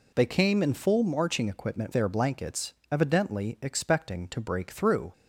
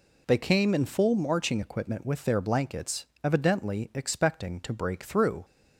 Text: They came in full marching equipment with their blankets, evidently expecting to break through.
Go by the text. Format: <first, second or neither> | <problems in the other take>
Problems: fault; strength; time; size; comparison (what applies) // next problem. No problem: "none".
second | skips "with"; at 1.9 s